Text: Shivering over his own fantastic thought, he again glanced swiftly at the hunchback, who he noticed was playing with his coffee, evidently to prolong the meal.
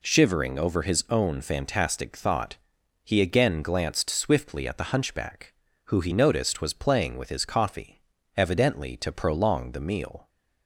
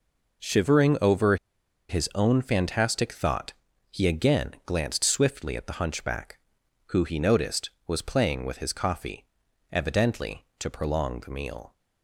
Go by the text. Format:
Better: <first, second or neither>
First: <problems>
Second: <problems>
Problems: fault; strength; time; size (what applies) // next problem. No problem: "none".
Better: first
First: none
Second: pauses between "over" and "his"; noticeable; at 1.3 s; 0.53 s long